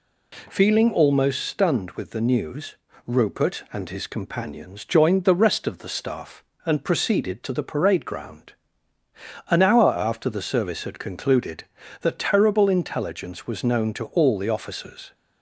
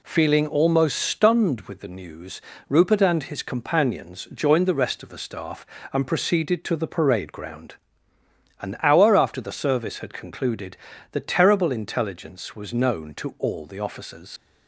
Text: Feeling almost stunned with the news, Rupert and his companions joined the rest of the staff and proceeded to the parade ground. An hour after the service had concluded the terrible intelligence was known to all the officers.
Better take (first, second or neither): first